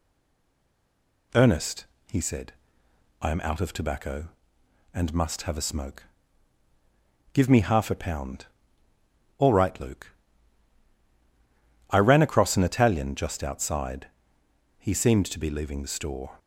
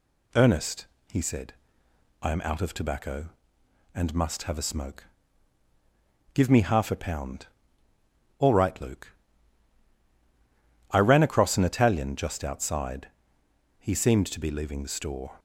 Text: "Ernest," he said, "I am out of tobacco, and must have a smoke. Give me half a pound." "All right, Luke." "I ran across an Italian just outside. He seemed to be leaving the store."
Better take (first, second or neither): second